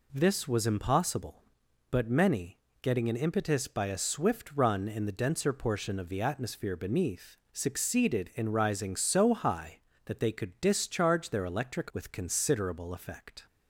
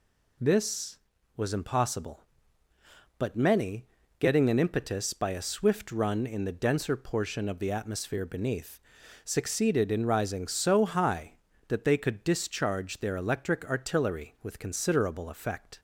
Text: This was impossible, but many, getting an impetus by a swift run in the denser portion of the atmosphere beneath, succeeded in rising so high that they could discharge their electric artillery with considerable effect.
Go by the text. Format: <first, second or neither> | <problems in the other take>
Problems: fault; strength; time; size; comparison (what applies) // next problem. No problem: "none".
second | skips "artillery"; at 11.9 s